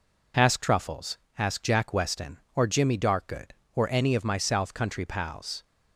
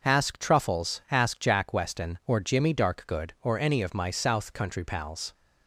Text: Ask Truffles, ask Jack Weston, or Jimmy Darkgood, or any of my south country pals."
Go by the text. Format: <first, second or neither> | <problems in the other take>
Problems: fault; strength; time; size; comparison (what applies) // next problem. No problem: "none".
neither | none